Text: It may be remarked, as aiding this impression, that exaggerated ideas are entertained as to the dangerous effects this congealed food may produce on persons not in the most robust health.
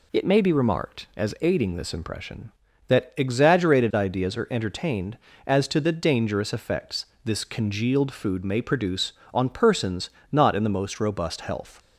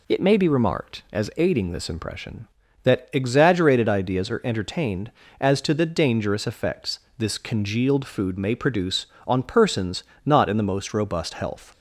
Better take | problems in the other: neither | pauses between "effects" and "this"; slight; the same in both // pauses between "persons" and "not"; slight; the same in both

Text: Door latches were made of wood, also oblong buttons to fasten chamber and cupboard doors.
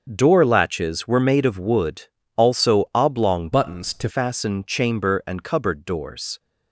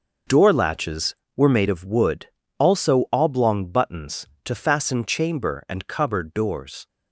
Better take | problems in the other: second | starts louder than the rest; noticeable; until 1.0 s; 6 dB // changes voice from "buttons" to "to"; from 3.5 to 4.0 s; 0.5 s long

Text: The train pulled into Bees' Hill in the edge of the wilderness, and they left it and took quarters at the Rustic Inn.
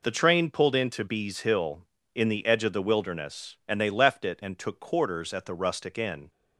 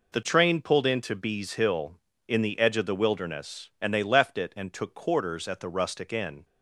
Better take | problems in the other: neither | none

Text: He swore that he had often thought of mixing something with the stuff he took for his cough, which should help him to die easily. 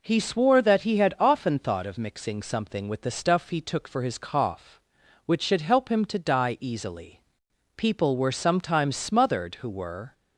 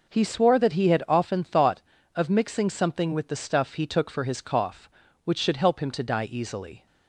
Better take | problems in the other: second | goes on to say "People were sometimes smothered who were"; strong; from 7.7 s on; 2.3 s long

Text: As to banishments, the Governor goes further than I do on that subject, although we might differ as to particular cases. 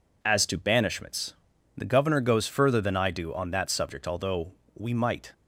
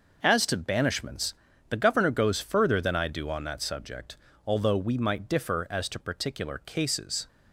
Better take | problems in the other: second | pauses between "although" and "we"; slight; at 4.5 s; 0.22 s long // stops before "differ as to particular cases"; at 5.3 s

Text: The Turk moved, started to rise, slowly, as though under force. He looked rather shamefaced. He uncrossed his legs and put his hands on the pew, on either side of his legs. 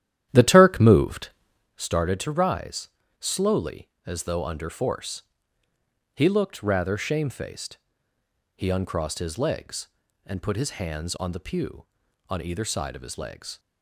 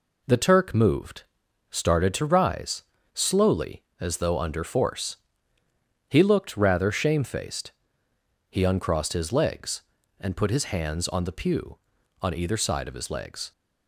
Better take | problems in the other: second | starts louder than the rest; strong; until 1.8 s; 11.5 dB

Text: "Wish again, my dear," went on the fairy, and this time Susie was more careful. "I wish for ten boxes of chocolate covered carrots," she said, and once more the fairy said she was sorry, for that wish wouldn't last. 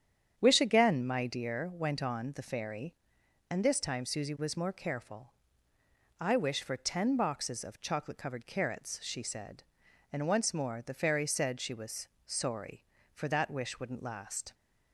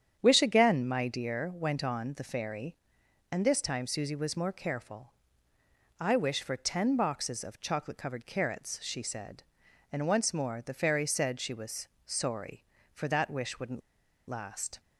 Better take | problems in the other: first | starts louder than the rest; strong; until 1.2 s; 9 dB; strong in the first // pauses between "was" and "sorry"; slight; at 11.8 s; 0.18 s long; slight in the first // pauses between "wouldn't" and "last"; noticeable; at 13.8 s; 0.49 s long

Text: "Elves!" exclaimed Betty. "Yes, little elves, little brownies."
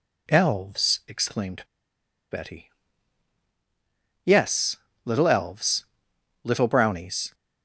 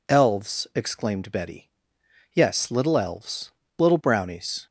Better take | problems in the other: second | pauses between "exclaimed" and "Betty"; noticeable; at 1.6 s; 0.67 s long

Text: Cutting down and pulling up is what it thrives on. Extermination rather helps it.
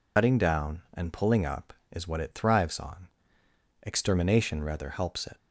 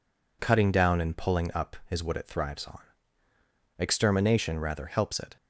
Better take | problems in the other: second | loses the start of "Cutting"; at 0.1 s; 110 ms

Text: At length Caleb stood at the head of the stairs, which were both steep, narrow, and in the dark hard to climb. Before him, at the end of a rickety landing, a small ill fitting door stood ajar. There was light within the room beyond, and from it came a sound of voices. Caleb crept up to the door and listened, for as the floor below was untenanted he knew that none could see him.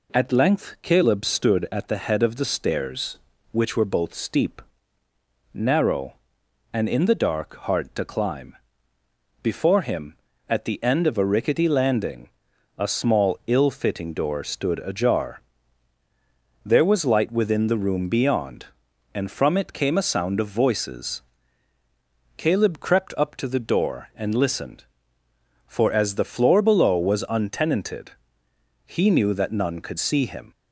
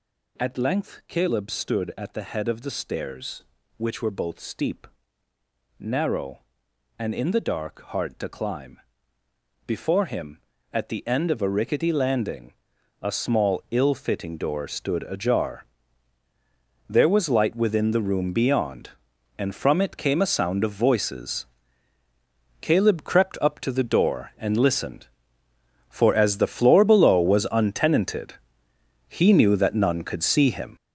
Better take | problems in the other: first | gets louder; strong; throughout; 8.5 dB // pauses between "untenanted" and "he"; noticeable; at 28.3 s; 0.74 s long; noticeable in the first

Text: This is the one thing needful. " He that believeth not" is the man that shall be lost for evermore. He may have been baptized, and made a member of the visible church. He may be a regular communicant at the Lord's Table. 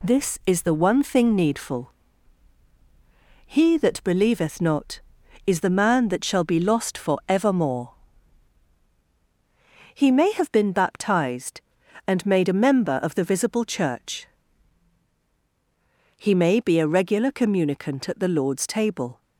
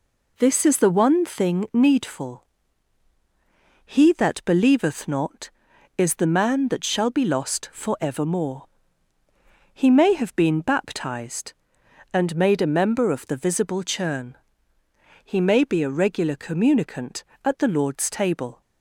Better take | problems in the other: first | says "churn" for "church"; at 13.8 s

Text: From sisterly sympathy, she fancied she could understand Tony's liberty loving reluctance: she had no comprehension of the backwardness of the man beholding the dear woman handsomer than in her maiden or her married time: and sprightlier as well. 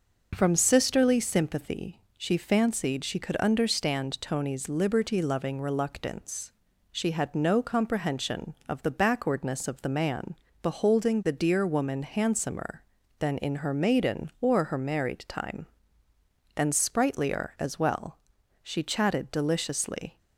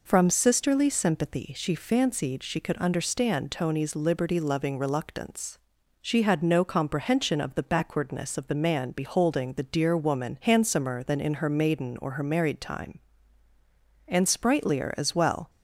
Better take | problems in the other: second | pauses between "man" and "beholding"; slight; at 10.3 s; 0.30 s long // goes on to say "She chatted deliciously"; from 18.6 s on; 1.5 s long

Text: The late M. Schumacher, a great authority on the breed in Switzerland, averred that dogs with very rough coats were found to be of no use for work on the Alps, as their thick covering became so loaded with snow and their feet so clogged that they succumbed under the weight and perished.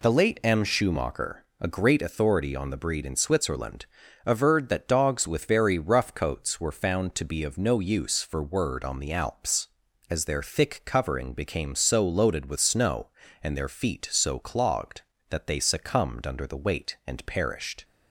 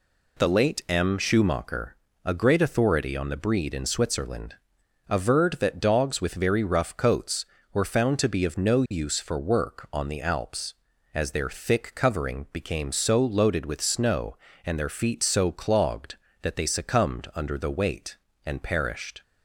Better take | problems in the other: second | says "word" for "work"; at 8.4 s

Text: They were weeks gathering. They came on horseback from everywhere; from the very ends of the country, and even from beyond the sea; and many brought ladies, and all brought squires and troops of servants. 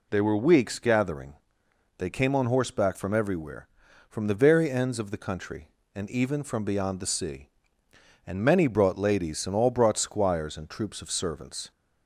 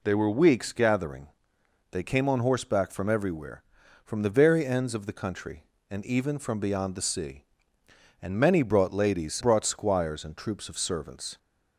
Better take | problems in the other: first | skips "and all"; at 9.4 s

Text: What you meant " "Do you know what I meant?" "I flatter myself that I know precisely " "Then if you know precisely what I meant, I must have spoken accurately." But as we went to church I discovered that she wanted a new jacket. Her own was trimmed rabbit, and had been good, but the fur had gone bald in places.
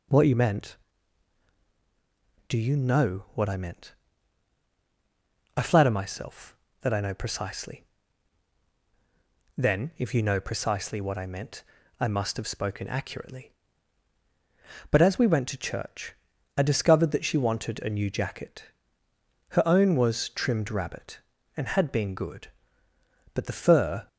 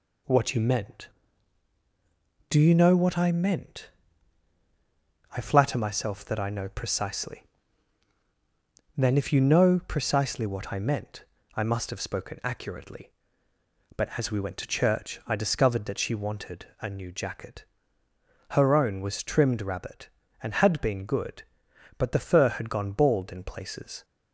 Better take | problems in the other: second | pauses between "church" and "I"; at 16.1 s; 0.42 s long // stops before "had gone bald in places"; at 24.0 s

